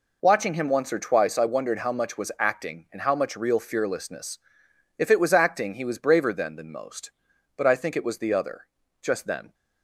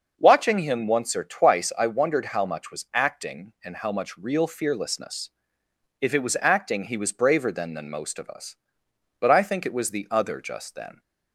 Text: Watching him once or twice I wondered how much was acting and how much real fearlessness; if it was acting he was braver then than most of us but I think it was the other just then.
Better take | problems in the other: second | skips "of us"; at 7.3 s // pauses between "other" and "just"; slight; at 8.6 s; 0.34 s long

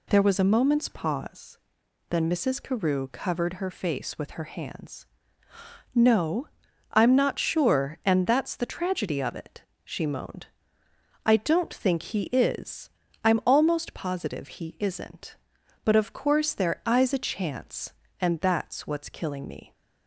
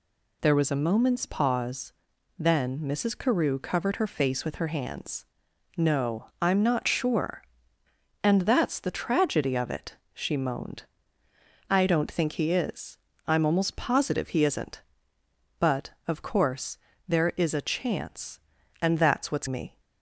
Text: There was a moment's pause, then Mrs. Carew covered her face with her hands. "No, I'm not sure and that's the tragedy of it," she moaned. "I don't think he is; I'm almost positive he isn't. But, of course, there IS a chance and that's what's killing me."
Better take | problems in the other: first | skips "killing"; at 19.4 s

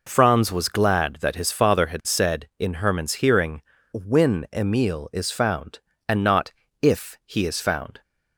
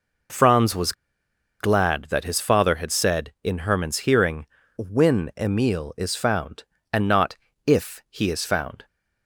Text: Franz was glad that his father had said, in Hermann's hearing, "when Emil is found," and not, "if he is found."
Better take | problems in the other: first | pauses between "was" and "glad"; noticeable; at 0.9 s; 0.67 s long

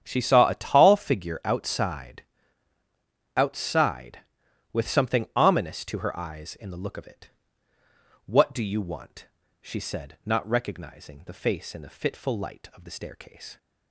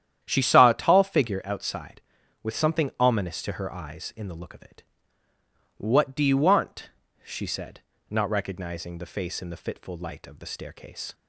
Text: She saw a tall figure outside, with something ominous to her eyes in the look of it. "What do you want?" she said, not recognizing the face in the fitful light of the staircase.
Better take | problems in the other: second | starts louder than the rest; strong; until 1.0 s; 9 dB; strong in the second // says "outside" twice; at 3.3 s

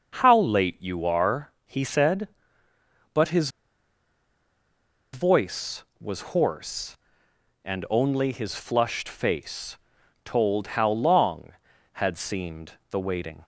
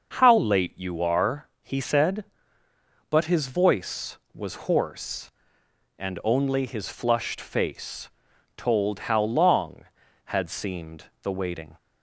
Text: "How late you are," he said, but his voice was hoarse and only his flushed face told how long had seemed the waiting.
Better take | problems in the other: second | starts louder than the rest; noticeable; until 1.1 s; 6 dB; also in the second // pauses between "his" and "voice"; strong; at 3.4 s; 1.6 s long // pauses between "face" and "told"; noticeable; at 9.7 s; 0.48 s long; noticeable in the second

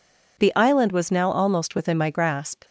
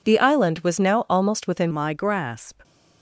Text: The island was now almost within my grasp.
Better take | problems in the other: first | changes voice at "my"; from 1.7 s on; 0.9 s long

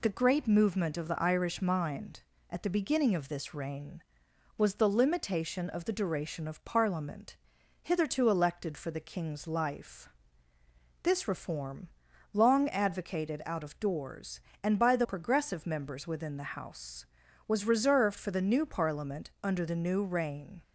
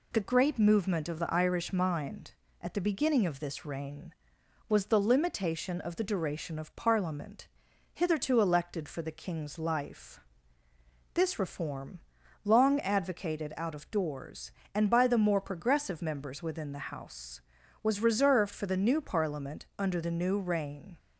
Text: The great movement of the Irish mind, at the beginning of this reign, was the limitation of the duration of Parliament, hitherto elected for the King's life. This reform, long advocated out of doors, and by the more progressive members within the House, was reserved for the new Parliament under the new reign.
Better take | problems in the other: second | skips "more"; at 15.0 s

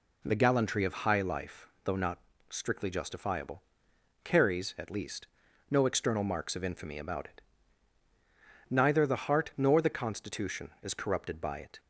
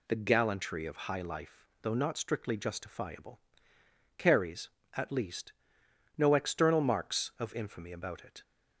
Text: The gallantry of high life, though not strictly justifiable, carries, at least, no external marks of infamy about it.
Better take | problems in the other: second | pauses between "not" and "strictly"; slight; at 2.1 s; 0.32 s long // goes on to say "Neither the heart nor the constitution is corrupted by it"; strong; from 8.6 s on; 3.1 s long

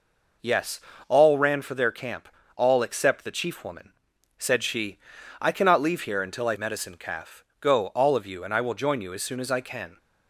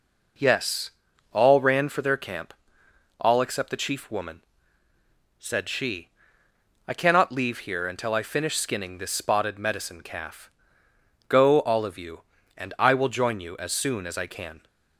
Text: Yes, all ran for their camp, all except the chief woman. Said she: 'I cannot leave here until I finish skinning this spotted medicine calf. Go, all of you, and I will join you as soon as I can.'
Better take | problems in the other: second | skips "finish skinning this spotted"; at 6.5 s

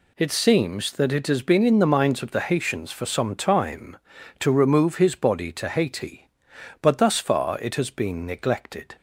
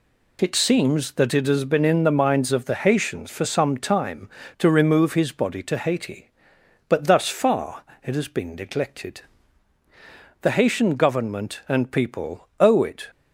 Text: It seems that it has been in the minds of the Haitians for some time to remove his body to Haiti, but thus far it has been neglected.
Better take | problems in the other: first | pauses between "far" and "it"; slight; at 7.8 s; 0.20 s long // goes on to say "The Haitian Government and people owe it"; strong; from 10.3 s on; 2.6 s long

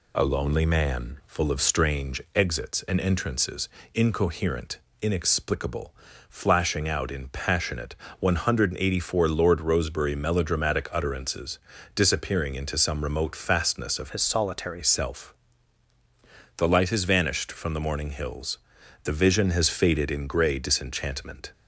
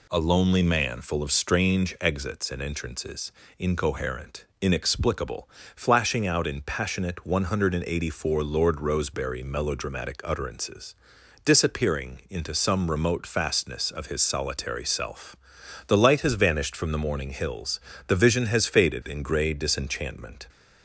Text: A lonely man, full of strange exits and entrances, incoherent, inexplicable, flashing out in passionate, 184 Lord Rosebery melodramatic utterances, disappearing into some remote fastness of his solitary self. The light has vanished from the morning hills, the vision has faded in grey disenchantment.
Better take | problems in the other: second | changes voice from "his" to "solitary"; from 14.0 to 14.8 s; 0.8 s long

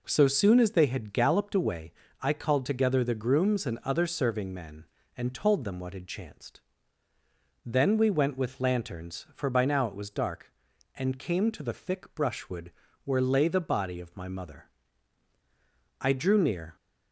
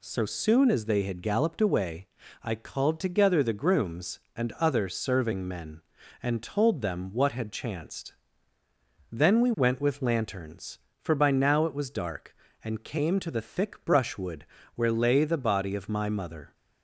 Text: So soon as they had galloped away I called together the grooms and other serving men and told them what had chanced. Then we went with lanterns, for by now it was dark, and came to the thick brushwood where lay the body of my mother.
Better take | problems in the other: second | pauses between "away" and "I"; slight; at 1.9 s; 0.30 s long; slight in the second // pauses between "brushwood" and "where"; slight; at 12.7 s; 0.32 s long; slight in the second // goes on to say "I drew near"; noticeable; from 15.9 s on; 0.76 s long

